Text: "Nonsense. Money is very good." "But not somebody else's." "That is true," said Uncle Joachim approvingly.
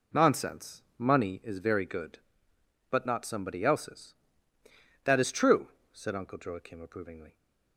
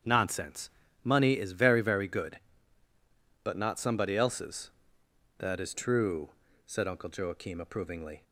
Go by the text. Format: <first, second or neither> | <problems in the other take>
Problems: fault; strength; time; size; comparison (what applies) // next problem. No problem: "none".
first | starts louder than the rest; strong; until 1.3 s; 8 dB // says "very" twice; at 1.8 s